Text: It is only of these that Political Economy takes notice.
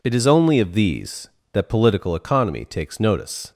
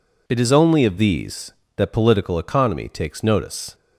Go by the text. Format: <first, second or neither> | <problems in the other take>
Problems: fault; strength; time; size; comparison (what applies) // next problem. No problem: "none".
neither | none